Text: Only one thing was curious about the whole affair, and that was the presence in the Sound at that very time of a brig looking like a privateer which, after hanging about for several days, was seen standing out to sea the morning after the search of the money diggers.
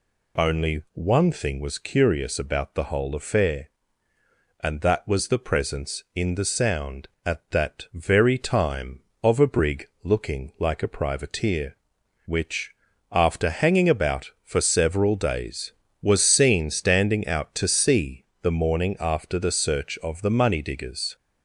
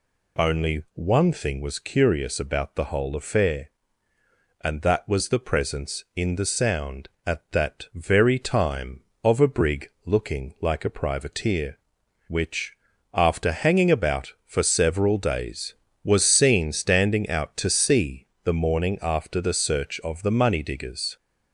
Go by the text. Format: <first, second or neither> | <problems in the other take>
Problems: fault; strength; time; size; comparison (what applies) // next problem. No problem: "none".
neither | pauses between "brig" and "looking"; slight; the same in both // pauses between "sea" and "the"; slight; the same in both